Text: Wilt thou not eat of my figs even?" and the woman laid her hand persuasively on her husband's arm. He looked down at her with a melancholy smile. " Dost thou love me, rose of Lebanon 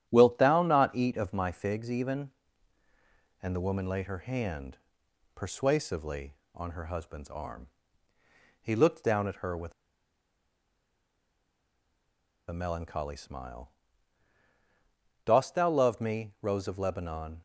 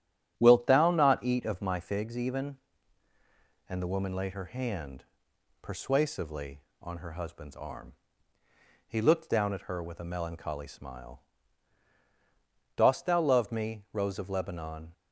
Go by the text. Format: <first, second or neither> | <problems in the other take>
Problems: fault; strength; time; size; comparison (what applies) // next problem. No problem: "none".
second | starts louder than the rest; strong; until 1.0 s; 11 dB; strong in the second // pauses between "hand" and "persuasively"; noticeable; at 4.7 s; 0.58 s long; noticeable in the second // pauses between "with" and "a"; strong; at 9.7 s; 2.7 s long